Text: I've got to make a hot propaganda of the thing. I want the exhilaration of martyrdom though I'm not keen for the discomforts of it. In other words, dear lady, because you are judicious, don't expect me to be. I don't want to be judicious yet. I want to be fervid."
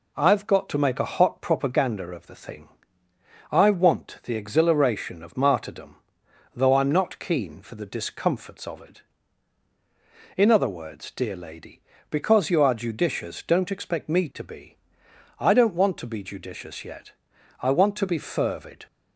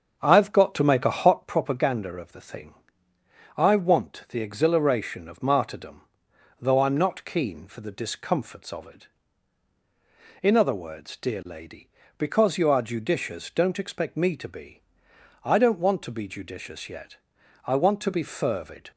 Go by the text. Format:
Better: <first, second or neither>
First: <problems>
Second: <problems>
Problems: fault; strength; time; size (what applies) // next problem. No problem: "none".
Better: first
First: pauses between "martyrdom" and "though"; noticeable; at 5.9 s; 0.60 s long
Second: starts louder than the rest; until 1.4 s; 7 dB // pauses between "martyrdom" and "though"; noticeable; at 6.0 s; 0.60 s long